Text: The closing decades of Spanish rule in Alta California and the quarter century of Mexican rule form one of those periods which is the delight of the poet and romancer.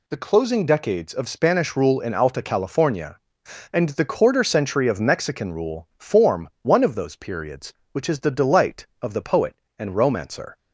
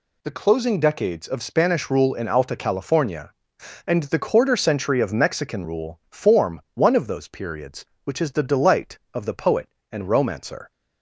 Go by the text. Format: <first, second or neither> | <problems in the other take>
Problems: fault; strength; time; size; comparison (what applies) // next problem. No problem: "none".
neither | none